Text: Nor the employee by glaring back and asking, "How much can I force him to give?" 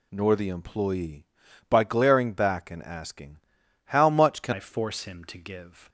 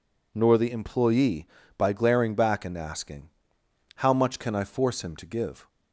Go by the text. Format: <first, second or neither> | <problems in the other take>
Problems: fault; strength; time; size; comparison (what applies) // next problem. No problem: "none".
second | changes voice at "I"; from 4.5 s on; 1.3 s long